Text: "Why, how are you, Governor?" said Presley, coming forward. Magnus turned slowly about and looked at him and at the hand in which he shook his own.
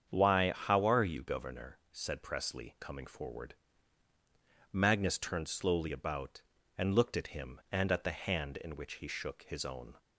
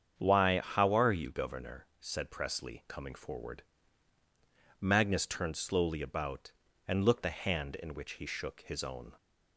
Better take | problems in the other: first | starts louder than the rest; strong; until 1.2 s; 7.5 dB; strong in the first // skips "at him and at"; at 7.2 s

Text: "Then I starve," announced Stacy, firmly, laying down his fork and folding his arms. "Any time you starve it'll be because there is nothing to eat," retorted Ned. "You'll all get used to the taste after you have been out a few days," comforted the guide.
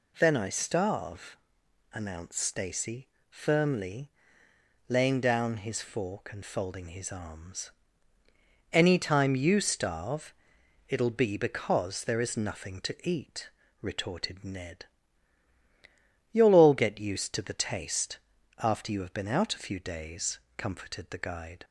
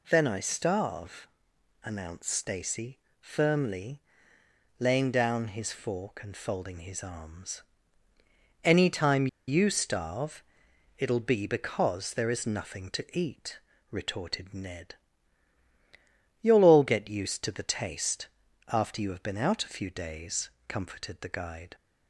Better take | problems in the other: first | pauses between "time" and "you"; slight; at 9.2 s; 0.21 s long // pauses between "starve" and "it'll"; noticeable; at 10.4 s; 0.54 s long; noticeable in the first // pauses between "taste" and "after"; at 18.2 s; 0.40 s long; also in the first

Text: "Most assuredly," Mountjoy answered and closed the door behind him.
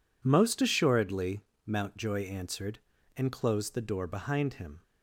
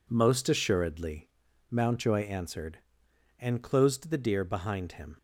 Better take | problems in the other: first | says "deer" for "door"; at 4.1 s

